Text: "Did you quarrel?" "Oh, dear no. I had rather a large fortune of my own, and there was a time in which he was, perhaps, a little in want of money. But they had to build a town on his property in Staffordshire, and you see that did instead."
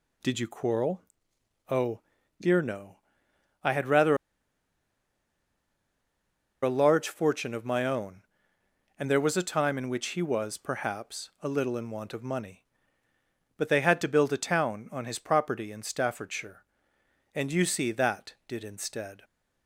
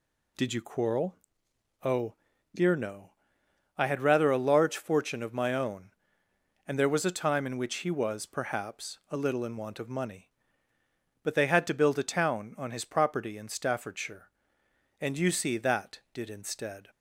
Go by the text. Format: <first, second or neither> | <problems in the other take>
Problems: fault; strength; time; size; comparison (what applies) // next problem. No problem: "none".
second | pauses between "rather" and "a"; strong; at 4.1 s; 2.4 s long